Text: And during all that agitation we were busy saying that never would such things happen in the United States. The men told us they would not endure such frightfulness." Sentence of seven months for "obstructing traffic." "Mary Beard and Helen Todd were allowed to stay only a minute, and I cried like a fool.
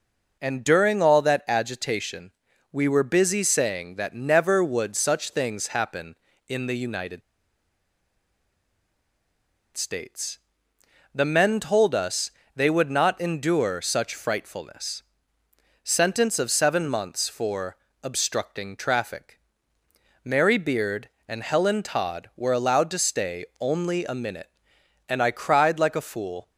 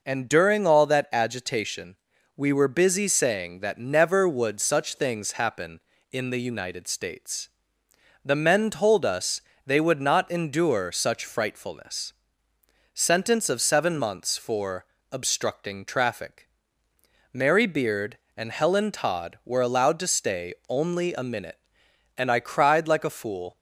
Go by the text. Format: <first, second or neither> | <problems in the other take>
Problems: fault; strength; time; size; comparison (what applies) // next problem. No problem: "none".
second | pauses between "agitation" and "we"; at 2.3 s; 0.40 s long; also in the second // pauses between "United" and "States"; strong; at 7.2 s; 2.5 s long // pauses between "us" and "they"; slight; at 12.3 s; 0.24 s long; slight in the second // pauses between "for" and "obstructing"; slight; at 17.7 s; 0.24 s long; slight in the second